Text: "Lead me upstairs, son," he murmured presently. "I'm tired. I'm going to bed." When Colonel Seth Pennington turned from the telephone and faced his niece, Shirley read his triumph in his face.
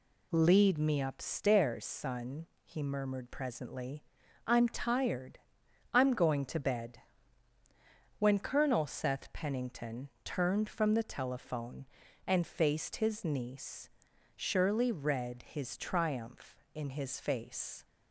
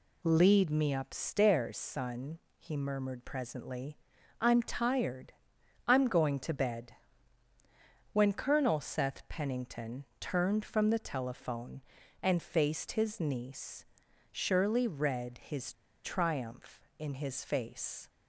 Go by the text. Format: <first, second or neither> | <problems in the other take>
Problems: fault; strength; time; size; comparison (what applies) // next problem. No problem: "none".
first | pauses between "Pennington" and "turned"; slight; at 10.0 s; 0.16 s long; slight in the first // pauses between "his" and "triumph"; slight; at 15.7 s; 0.31 s long